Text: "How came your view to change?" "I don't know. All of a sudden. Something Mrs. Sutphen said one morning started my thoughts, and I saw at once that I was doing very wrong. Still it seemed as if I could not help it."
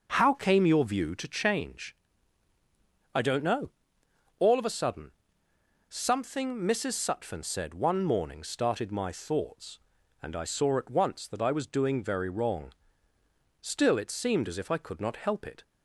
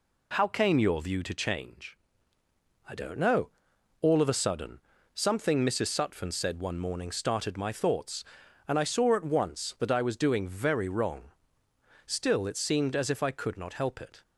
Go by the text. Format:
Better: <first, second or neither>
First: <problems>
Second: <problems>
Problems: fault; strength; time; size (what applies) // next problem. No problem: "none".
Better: neither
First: none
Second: none